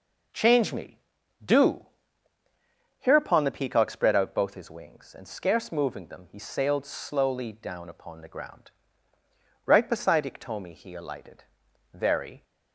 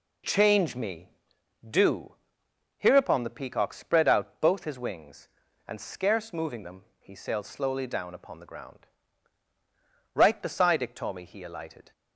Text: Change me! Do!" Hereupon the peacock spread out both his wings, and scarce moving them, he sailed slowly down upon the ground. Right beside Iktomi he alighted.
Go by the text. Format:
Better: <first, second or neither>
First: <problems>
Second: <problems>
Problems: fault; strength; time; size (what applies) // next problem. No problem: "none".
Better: second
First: goes on to say "Very"; from 11.9 s on; 0.50 s long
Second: none